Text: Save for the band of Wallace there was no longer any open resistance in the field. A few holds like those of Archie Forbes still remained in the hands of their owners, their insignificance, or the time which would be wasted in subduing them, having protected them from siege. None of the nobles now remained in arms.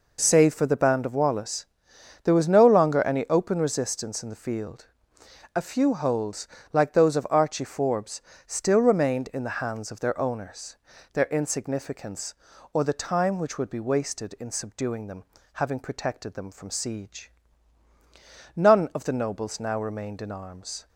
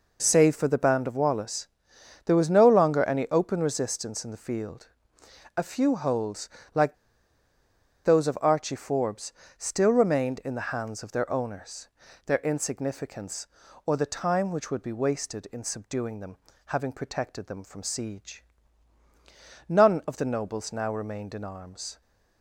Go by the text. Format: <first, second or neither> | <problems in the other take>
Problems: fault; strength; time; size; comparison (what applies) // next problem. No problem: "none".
first | pauses between "Wallace" and "there"; noticeable; at 1.6 s; 0.58 s long; noticeable in the first // pauses between "holds" and "like"; slight; at 6.4 s; 0.28 s long; slight in the first // pauses between "like" and "those"; at 6.9 s; 1.1 s long // pauses between "Forbes" and "still"; slight; at 9.3 s; 0.26 s long; slight in the first